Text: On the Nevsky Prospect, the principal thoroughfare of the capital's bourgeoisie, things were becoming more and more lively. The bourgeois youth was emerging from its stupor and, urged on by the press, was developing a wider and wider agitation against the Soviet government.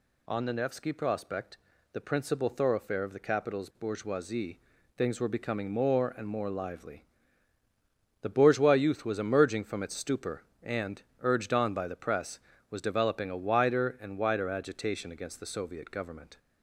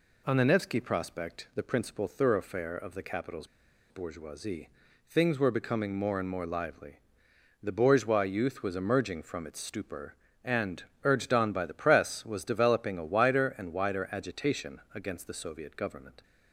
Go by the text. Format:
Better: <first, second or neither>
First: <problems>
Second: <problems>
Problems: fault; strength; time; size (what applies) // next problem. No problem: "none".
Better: first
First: none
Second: pauses between "capital's" and "bourgeoisie"; at 3.4 s; 0.44 s long